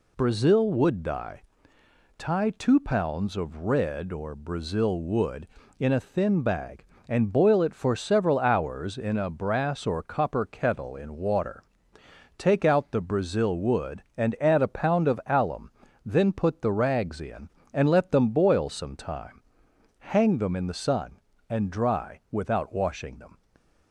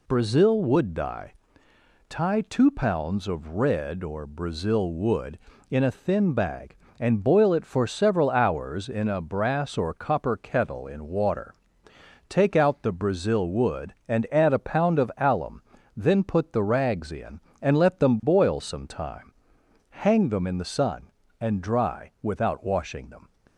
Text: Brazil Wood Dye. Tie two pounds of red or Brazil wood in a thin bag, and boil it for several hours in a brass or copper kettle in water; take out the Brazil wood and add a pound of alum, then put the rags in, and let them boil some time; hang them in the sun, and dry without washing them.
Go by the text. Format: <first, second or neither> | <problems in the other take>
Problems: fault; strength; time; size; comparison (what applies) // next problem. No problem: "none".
neither | none